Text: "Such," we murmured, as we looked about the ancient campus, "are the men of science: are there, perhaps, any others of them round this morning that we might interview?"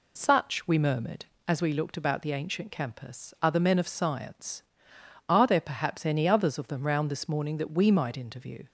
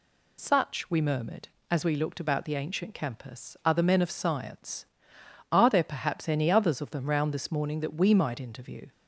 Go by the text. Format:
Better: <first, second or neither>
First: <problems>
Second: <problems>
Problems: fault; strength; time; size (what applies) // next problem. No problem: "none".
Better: second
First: starts louder than the rest; slight; until 1.5 s; 2.5 dB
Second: none